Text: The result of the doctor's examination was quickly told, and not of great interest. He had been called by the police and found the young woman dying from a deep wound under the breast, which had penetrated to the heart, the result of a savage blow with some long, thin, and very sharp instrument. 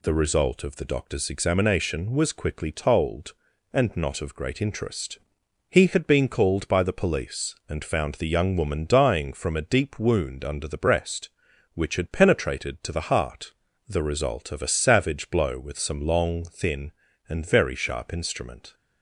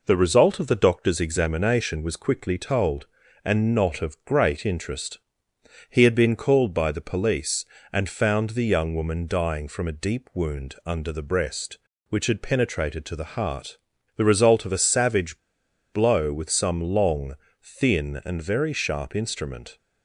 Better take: first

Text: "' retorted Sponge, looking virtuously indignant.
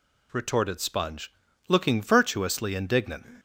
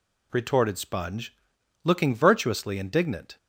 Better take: neither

